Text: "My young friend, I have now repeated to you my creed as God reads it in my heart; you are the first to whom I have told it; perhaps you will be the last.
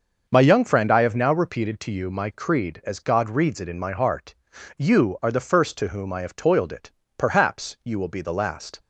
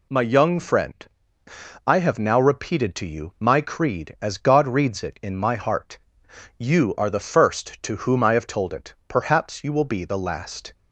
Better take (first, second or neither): second